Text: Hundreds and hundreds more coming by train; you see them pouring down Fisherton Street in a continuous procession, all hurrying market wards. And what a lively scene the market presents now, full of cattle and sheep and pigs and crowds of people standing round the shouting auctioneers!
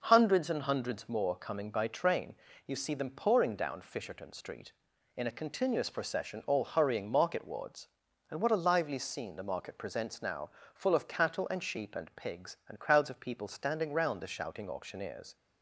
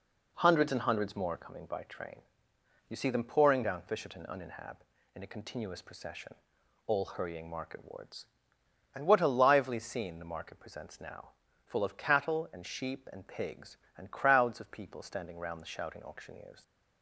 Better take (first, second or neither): first